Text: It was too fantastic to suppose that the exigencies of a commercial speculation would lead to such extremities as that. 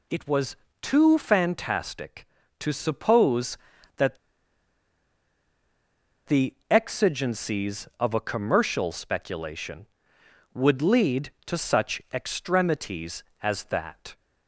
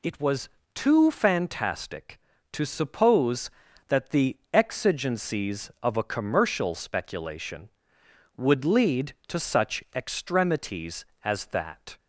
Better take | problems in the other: second | pauses between "was" and "too"; slight; at 0.5 s; 0.26 s long; slight in the second // pauses between "that" and "the"; strong; at 4.1 s; 2.1 s long // pauses between "the" and "exigencies"; slight; at 6.5 s; 0.16 s long; slight in the second

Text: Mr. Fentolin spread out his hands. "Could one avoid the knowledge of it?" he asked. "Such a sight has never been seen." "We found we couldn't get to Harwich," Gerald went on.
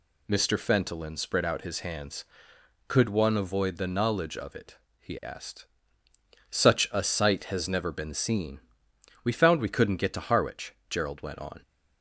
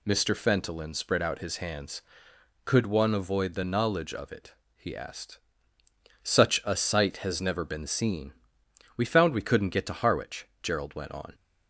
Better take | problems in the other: neither | none

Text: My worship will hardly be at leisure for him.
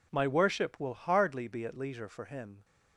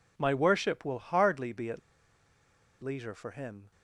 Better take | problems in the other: first | pauses between "at" and "leisure"; at 1.7 s; 1.0 s long

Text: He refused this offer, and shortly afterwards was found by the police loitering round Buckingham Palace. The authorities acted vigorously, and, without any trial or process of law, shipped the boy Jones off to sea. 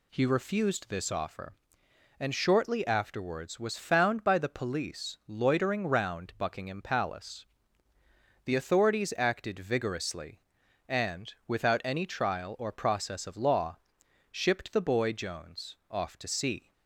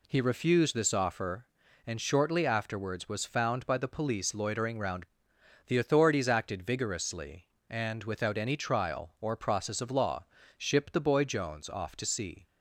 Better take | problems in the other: first | skips "Buckingham Palace"; at 5.3 s

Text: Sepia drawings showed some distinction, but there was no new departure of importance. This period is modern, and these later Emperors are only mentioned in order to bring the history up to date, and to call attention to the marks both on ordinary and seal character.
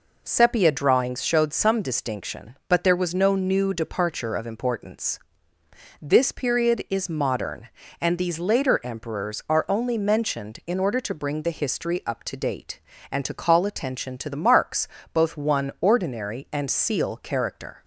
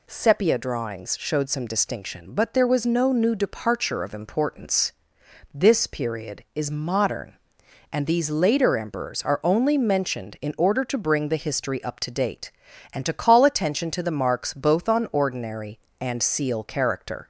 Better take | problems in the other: second | pauses between "marks" and "both"; slight; at 14.8 s; 0.26 s long // says "one" for "on"; at 15.3 s

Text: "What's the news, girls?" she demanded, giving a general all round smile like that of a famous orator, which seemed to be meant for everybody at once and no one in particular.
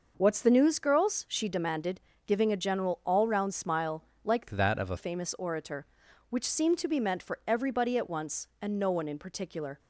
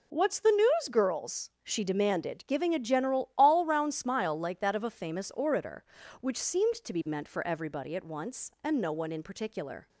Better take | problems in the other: second | pauses between "smile" and "like"; slight; at 4.0 s; 0.20 s long // changes voice from "that" to "a"; from 4.4 to 4.9 s; 0.5 s long

